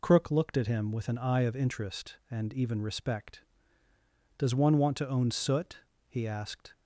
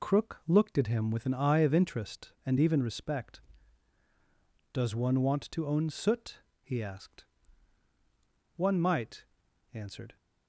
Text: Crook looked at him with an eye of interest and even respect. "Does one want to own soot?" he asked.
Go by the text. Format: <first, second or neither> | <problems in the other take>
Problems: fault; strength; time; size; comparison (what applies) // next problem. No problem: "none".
first | goes on to say "One might answered"; from 8.5 s on; 1.6 s long